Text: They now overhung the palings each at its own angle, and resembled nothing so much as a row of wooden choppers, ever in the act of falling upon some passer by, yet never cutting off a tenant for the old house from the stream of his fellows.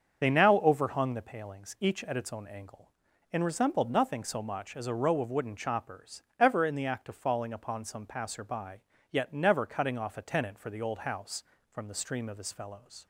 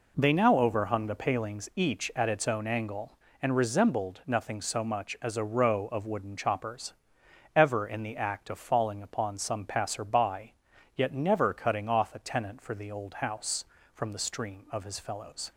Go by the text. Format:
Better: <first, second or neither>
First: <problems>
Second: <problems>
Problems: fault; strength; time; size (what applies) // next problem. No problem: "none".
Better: second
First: loses the start of "They"; at 0.2 s; 35 ms // starts louder than the rest; until 1.2 s; 7 dB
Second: none